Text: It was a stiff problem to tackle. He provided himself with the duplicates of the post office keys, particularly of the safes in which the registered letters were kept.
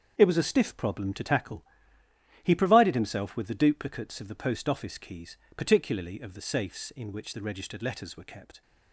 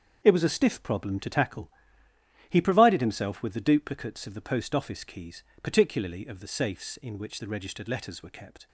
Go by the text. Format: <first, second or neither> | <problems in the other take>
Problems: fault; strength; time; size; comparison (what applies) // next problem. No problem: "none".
neither | starts louder than the rest; the same in both